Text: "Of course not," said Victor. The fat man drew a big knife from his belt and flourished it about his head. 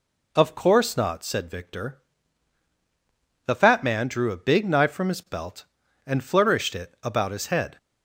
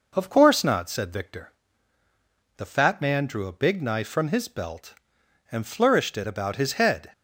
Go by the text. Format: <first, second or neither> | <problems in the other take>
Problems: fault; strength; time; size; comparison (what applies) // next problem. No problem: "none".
neither | none